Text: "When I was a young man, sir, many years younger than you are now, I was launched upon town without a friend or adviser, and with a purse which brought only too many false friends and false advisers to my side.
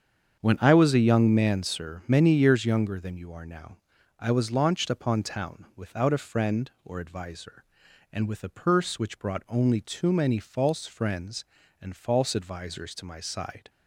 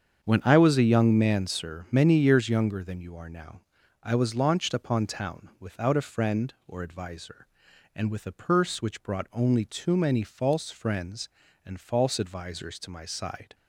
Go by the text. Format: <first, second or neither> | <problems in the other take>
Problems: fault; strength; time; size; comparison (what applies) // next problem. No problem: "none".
neither | starts louder than the rest; strong; the same in both